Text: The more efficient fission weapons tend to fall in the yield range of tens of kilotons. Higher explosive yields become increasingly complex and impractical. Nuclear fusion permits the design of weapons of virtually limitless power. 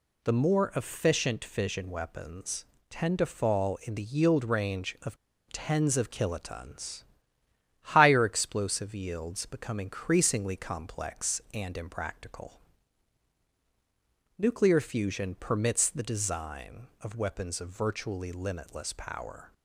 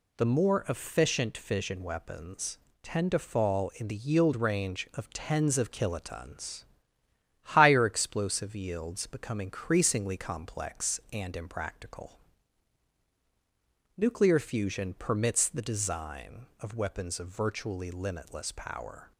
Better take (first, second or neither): second